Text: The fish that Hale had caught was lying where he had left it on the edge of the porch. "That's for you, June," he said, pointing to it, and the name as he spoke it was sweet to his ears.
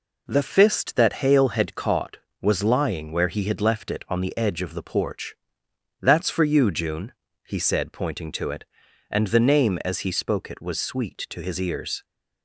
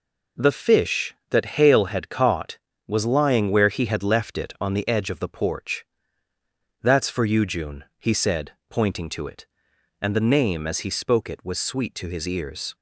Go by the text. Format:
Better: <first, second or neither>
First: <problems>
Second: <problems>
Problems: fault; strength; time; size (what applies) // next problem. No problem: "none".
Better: second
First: says "fist" for "fish"; at 0.4 s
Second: none